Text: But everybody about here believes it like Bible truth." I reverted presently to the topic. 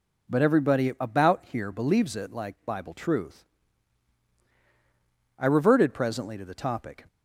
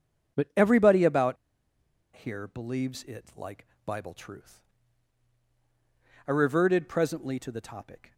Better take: first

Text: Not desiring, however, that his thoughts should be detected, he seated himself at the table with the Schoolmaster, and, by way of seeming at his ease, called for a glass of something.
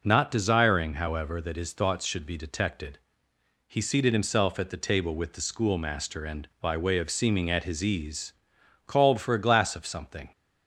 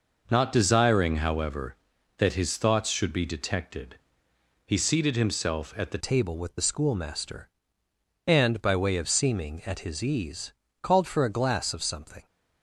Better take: first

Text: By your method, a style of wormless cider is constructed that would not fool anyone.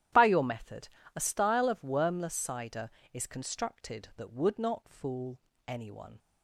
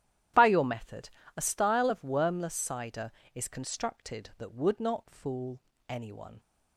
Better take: neither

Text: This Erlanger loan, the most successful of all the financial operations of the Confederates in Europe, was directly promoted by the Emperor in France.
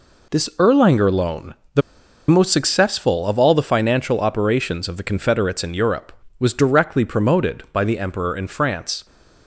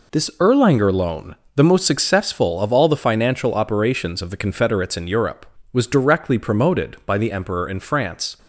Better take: second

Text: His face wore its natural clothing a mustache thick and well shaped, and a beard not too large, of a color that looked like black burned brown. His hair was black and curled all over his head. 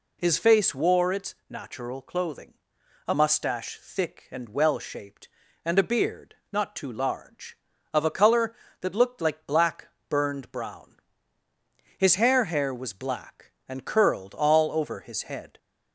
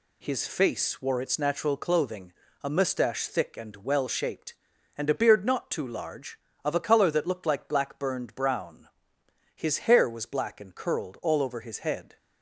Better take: second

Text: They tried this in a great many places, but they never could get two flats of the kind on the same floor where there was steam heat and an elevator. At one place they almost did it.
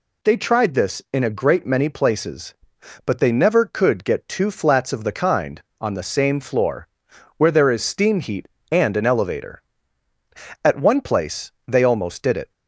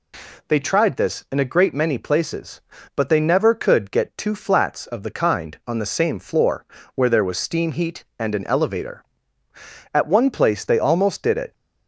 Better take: second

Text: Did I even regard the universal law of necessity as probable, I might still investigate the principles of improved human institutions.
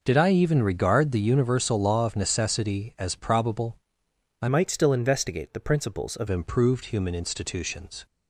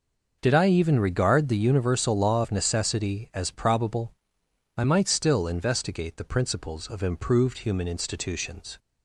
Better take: second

